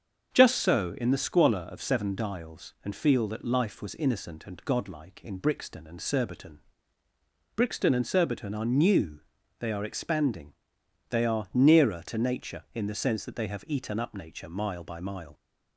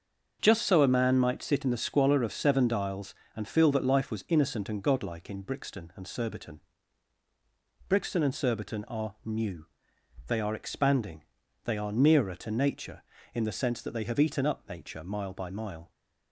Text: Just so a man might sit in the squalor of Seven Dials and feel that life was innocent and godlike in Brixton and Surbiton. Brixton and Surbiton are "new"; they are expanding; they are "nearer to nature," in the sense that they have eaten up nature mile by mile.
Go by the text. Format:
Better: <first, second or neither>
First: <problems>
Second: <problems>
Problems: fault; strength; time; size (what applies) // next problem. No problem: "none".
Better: second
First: starts louder than the rest; until 1.3 s; 7 dB // skips "a man might sit"; at 0.9 s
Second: starts louder than the rest; until 1.4 s; 7 dB